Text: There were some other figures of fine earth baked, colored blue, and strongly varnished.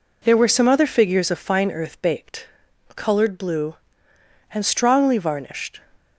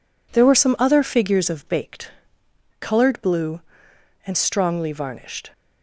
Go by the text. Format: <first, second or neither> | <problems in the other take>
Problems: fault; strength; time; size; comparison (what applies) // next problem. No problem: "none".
first | skips "fine earth"; at 1.6 s